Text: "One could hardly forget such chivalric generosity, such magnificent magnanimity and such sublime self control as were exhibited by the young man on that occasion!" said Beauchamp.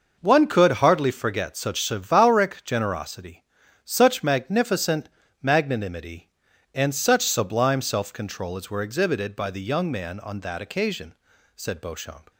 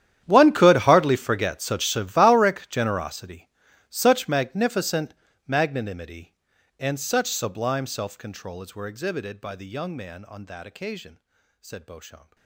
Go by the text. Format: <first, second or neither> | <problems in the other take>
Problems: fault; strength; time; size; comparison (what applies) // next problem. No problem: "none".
first | gets quieter; strong; throughout; 20.5 dB // pauses between "magnificent" and "magnanimity"; slight; at 5.1 s; 0.34 s long; slight in the first